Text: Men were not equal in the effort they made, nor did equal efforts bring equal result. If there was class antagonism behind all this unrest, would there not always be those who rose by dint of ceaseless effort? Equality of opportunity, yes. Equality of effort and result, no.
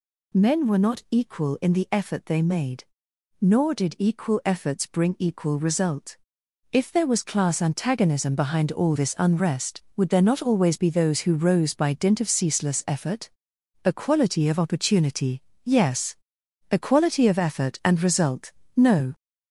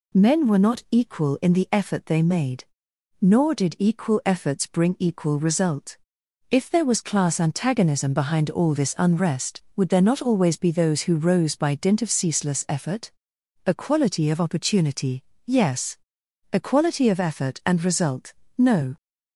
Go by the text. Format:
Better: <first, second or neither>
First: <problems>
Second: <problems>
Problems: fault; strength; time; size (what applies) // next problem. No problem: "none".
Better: second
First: gets louder; slight; throughout; 3 dB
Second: none